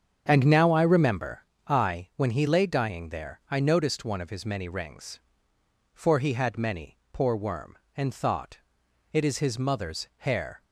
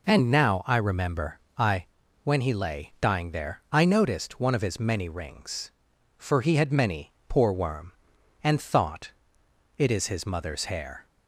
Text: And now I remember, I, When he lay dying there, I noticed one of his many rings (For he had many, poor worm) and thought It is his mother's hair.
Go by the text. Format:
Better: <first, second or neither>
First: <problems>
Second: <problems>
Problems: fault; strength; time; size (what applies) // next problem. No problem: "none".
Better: second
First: starts louder than the rest; strong; until 1.4 s; 7.5 dB // pauses between "thought" and "It"; noticeable; at 8.5 s; 0.56 s long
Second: pauses between "thought" and "It"; noticeable; at 9.1 s; 0.66 s long